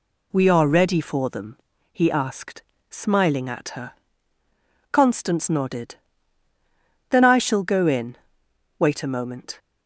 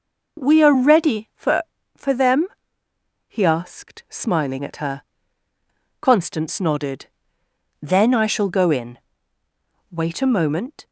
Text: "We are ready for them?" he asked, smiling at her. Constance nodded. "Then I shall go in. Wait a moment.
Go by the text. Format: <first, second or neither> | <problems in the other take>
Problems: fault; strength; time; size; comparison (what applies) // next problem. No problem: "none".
first | says "for" twice; at 1.9 s